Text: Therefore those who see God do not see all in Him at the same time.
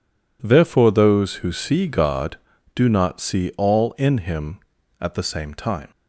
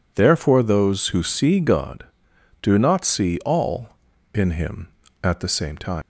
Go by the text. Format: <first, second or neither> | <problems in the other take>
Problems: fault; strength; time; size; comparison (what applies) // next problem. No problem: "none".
first | leaves "time" unfinished; at 6.0 s; 120 ms